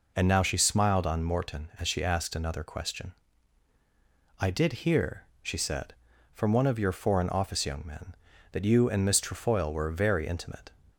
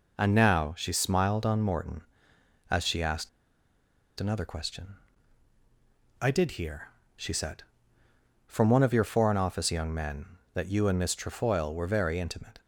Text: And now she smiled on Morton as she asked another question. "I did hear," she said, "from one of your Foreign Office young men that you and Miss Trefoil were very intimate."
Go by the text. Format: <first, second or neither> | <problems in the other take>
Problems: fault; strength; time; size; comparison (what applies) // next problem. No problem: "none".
first | pauses between "asked" and "another"; noticeable; at 3.2 s; 0.90 s long